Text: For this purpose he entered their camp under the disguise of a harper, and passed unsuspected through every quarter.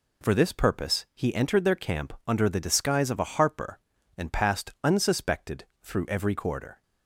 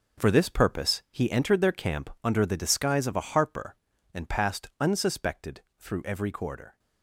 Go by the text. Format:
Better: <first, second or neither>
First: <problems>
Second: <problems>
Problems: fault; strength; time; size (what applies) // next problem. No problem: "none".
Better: first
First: pauses between "unsuspected" and "through"; slight; at 5.6 s; 0.18 s long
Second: gets quieter; strong; throughout; 12.5 dB // pauses between "unsuspected" and "through"; slight; at 5.6 s; 0.18 s long